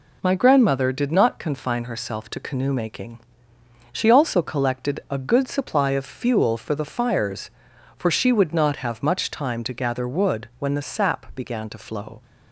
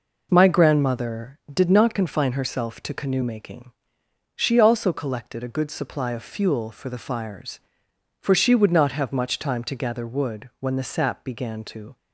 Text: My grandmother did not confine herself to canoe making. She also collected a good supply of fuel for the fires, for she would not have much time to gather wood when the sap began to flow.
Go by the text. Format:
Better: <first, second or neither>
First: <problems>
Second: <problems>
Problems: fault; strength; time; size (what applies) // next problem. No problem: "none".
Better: first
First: none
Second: stops before "flow"; at 11.9 s